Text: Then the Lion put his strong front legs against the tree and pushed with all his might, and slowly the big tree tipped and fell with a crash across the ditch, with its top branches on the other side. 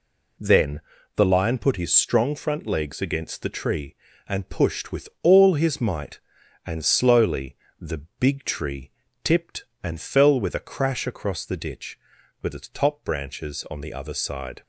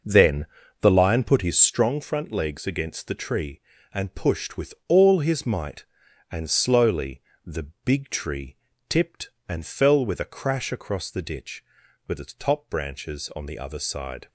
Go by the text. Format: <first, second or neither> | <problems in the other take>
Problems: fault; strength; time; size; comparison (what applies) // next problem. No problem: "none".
first | starts louder than the rest; noticeable; until 1.8 s; 6 dB // pauses between "Then" and "the"; slight; at 0.4 s; 0.36 s long; slight in the first // pauses between "slowly" and "the"; slight; at 7.2 s; 0.24 s long; slight in the first // pauses between "tree" and "tipped"; slight; at 8.5 s; 0.32 s long; slight in the first